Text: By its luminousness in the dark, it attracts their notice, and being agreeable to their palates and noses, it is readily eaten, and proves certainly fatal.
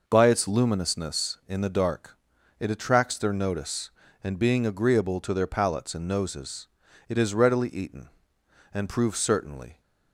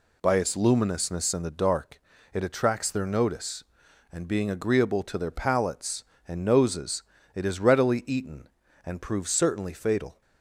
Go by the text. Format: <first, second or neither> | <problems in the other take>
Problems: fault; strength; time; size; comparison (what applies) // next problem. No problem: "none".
second | stops before "fatal"; at 9.7 s